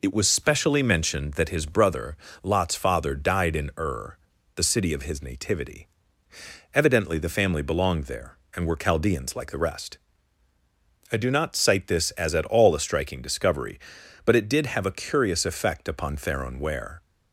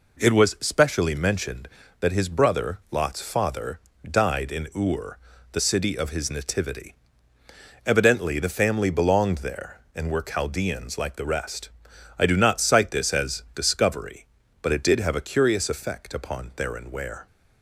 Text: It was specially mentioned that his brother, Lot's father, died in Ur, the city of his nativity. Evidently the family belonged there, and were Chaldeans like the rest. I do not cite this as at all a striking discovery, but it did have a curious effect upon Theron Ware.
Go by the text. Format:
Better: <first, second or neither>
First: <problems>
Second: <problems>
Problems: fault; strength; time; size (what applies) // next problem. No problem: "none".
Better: first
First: none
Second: skips "at all a striking"; at 13.4 s